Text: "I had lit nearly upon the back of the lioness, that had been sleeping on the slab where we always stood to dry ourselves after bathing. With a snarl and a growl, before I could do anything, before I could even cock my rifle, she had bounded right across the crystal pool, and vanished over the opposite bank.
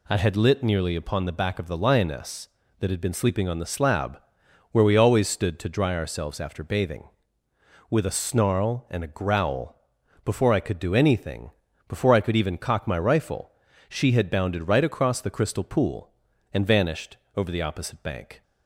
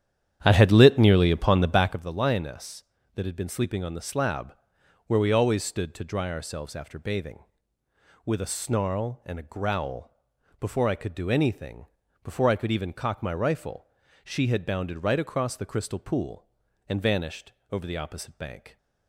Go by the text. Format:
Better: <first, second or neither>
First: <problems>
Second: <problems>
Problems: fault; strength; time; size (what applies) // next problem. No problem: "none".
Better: first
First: pauses between "slab" and "where"; noticeable; at 4.1 s; 0.52 s long // pauses between "vanished" and "over"; slight; at 17.1 s; 0.18 s long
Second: starts louder than the rest; strong; until 2.1 s; 9.5 dB // pauses between "slab" and "where"; noticeable; at 4.5 s; 0.52 s long // pauses between "vanished" and "over"; slight; at 17.5 s; 0.18 s long